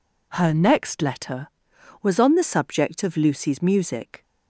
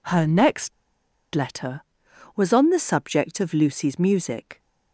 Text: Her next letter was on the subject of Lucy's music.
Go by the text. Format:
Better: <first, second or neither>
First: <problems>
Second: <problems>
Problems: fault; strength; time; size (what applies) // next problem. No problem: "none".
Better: first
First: none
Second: pauses between "next" and "letter"; noticeable; at 0.7 s; 0.62 s long